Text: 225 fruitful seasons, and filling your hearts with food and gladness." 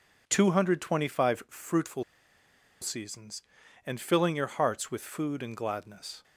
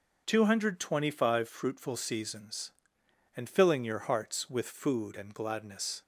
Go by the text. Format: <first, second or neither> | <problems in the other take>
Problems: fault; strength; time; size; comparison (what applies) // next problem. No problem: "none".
second | pauses between "fruitful" and "seasons"; noticeable; at 2.0 s; 0.78 s long